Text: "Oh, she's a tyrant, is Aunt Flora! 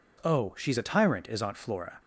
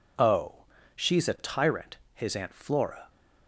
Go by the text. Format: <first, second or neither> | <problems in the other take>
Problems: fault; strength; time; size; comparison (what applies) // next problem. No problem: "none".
first | says "his" for "is"; at 2.1 s